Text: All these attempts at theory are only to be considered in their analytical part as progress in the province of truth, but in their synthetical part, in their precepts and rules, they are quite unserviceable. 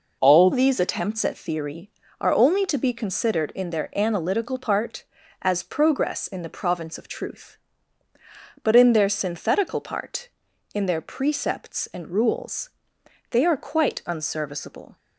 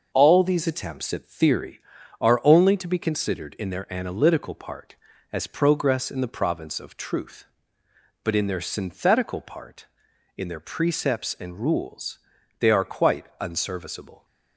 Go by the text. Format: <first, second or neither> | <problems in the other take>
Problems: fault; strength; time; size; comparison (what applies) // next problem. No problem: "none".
second | changes voice at "these"; from 0.5 s on; 14.4 s long